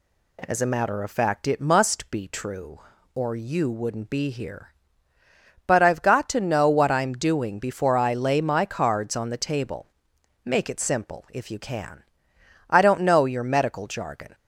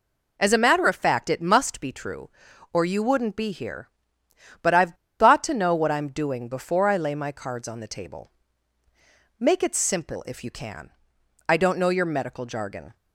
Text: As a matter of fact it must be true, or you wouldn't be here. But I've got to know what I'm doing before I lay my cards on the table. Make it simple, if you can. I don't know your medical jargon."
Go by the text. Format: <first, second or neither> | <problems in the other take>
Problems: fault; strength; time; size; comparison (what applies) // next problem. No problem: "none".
first | pauses between "I've" and "got"; slight; at 4.9 s; 0.25 s long